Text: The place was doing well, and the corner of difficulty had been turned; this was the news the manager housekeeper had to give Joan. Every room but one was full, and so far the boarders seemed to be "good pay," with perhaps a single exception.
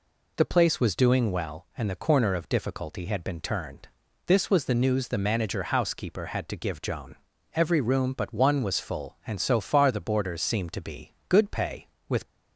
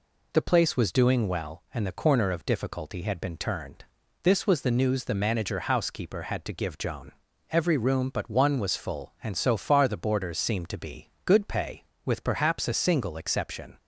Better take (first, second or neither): second